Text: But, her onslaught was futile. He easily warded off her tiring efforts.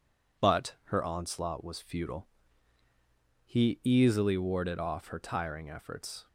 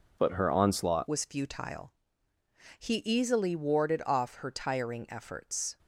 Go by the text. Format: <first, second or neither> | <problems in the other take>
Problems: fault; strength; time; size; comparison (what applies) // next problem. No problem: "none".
first | changes voice at "was"; from 1.0 s on; 4.7 s long